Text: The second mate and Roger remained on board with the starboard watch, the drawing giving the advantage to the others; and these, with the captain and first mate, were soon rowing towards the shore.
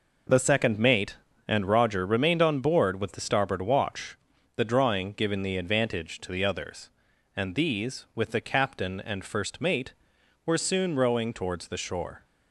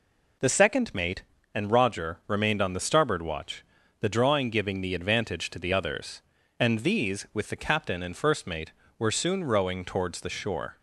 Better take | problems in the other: first | skips "board with"; at 2.7 s

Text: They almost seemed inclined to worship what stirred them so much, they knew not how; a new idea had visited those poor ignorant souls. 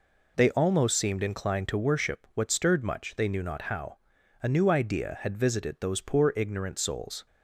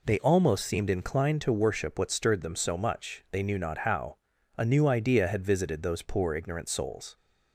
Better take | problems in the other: second | skips "them so"; at 2.8 s

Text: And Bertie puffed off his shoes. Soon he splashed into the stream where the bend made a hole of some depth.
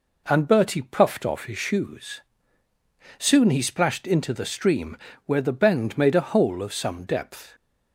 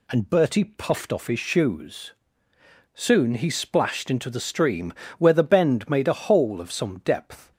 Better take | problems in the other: neither | pauses between "stream" and "where"; slight; the same in both

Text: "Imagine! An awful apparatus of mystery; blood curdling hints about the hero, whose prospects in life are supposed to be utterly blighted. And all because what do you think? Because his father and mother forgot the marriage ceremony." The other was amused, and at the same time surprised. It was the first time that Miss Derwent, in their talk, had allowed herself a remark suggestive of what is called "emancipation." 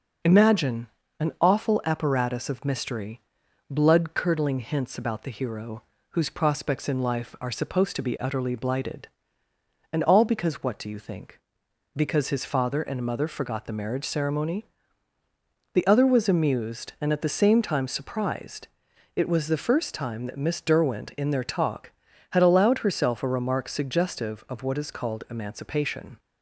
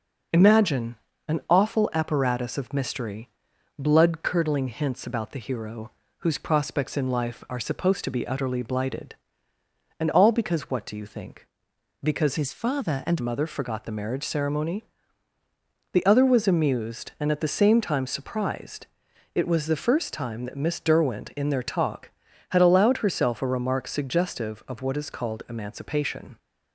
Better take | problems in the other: first | changes voice from "his" to "and"; from 12.3 to 13.2 s; 0.9 s long

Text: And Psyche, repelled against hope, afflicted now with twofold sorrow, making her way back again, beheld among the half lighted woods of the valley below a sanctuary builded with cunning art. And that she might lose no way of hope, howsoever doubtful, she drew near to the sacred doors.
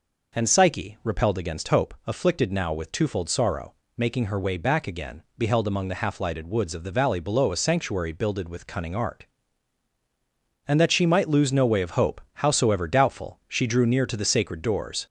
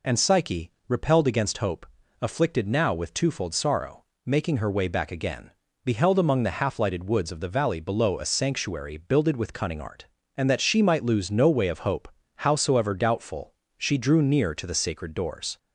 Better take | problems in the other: second | gets louder; slight; throughout; 3 dB

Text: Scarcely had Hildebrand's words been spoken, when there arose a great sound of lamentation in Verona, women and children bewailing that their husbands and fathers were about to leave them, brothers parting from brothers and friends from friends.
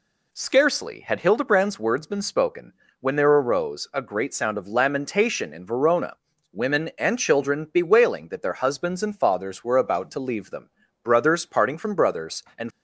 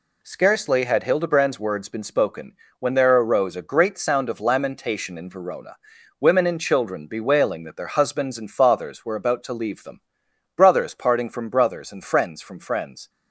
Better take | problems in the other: second | stops before "friends from friends"; at 12.7 s

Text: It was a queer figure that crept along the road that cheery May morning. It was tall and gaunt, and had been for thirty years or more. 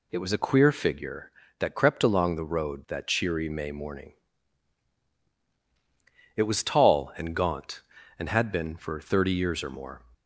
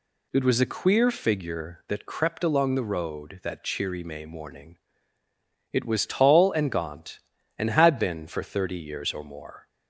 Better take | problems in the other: neither | none

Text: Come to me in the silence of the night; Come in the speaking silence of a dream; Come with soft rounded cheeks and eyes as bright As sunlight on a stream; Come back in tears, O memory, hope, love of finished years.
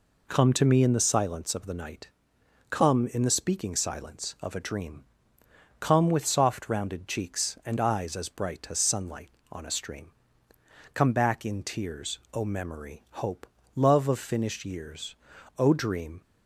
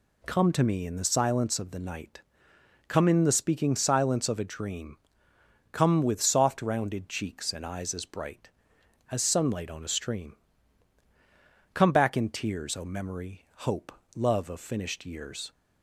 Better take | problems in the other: second | goes on to say "O dream"; noticeable; from 15.5 s on; 0.64 s long

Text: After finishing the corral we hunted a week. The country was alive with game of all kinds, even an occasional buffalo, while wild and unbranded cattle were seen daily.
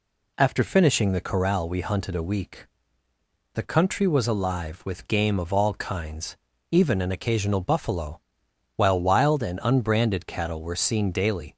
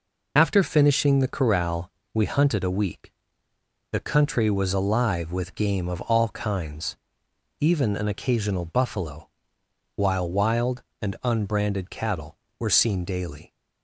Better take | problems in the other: first | loses the start of "After"; at 0.3 s; 65 ms // pauses between "corral" and "we"; slight; at 1.9 s; 0.22 s long

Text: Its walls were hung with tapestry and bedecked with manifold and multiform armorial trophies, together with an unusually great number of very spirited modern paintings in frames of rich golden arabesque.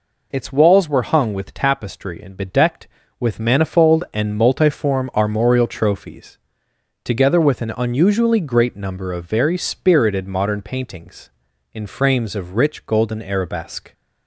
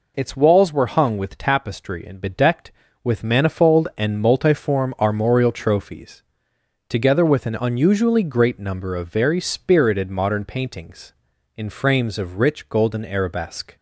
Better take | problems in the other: neither | none

